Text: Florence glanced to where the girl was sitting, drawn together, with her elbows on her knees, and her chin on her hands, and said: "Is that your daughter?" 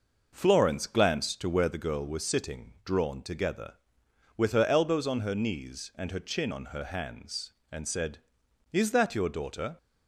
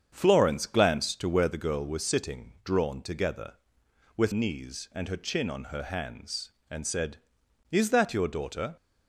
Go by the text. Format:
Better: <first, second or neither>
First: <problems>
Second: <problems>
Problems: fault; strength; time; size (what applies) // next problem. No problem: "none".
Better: first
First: none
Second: starts louder than the rest; strong; until 1.1 s; 7.5 dB // skips "her elbows on her"; at 4.3 s